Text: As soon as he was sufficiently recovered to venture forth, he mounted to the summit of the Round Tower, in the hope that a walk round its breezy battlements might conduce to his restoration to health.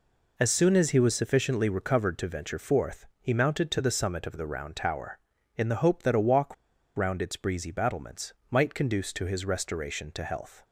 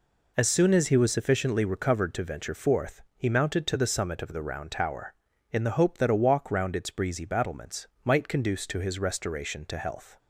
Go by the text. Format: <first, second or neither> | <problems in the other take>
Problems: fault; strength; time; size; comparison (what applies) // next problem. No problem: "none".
second | pauses between "walk" and "round"; at 6.5 s; 0.41 s long // pauses between "battlements" and "might"; slight; at 8.3 s; 0.20 s long; slight in the second